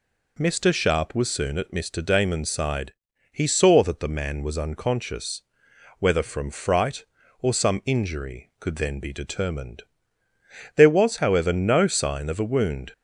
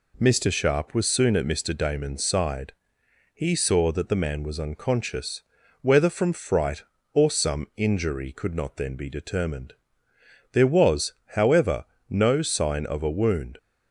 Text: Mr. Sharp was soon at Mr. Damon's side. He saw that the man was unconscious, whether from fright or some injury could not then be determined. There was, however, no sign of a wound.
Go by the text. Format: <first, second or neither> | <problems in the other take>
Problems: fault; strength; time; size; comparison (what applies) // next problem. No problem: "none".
second | skips "not"; at 8.7 s